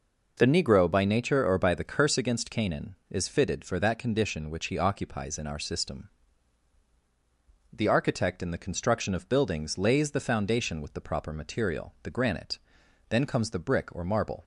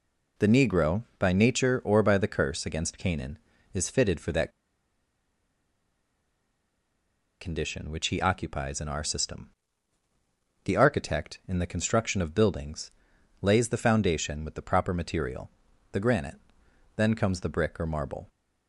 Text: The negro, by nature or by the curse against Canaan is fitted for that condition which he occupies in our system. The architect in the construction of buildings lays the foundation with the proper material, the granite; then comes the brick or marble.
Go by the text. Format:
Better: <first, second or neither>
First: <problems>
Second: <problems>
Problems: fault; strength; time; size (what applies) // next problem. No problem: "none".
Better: first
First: none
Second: pauses between "that" and "condition"; strong; at 4.5 s; 2.9 s long // pauses between "buildings" and "lays"; noticeable; at 12.9 s; 0.50 s long